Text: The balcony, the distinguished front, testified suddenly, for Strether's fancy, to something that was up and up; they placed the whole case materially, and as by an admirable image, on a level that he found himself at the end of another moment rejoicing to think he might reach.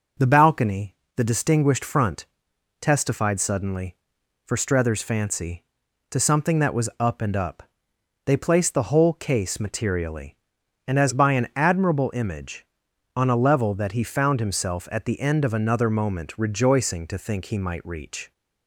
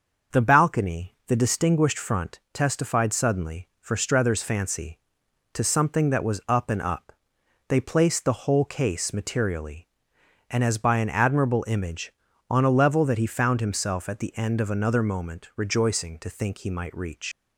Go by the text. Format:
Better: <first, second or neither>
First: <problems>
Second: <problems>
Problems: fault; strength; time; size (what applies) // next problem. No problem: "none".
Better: first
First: none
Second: starts louder than the rest; until 1.4 s; 6 dB // leaves "reach" unfinished; at 17.3 s; 110 ms